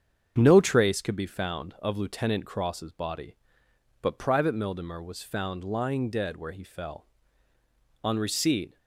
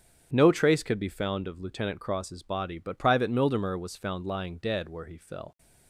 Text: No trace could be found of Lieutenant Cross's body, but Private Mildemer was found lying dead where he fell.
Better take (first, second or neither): second